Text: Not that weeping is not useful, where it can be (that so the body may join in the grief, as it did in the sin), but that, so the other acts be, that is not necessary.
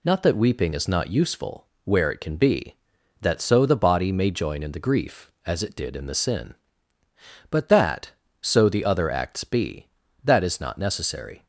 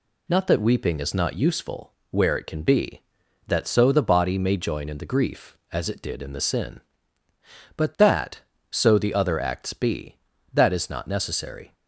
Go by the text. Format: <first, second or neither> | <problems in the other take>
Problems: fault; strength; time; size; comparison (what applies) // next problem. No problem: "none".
neither | none